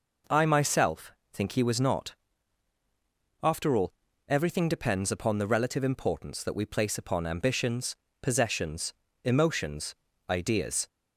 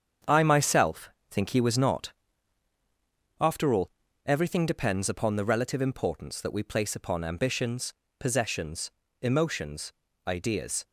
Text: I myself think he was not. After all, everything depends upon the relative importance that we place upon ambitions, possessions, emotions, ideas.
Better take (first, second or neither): first